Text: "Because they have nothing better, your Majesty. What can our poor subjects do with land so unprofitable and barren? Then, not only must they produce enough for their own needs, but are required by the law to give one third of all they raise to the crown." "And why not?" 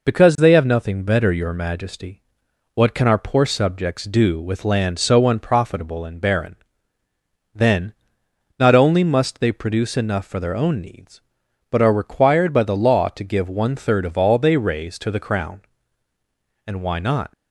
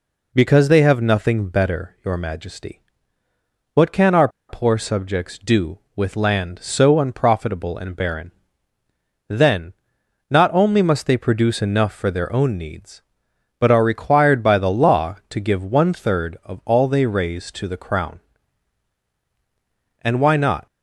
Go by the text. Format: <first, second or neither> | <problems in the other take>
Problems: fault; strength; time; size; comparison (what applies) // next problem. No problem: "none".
first | pauses between "our" and "poor"; slight; at 4.2 s; 0.20 s long